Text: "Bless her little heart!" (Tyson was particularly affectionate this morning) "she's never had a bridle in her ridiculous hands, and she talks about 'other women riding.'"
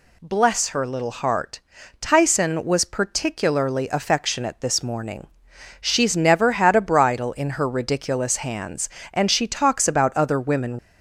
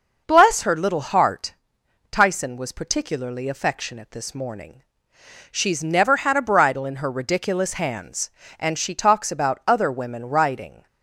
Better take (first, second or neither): second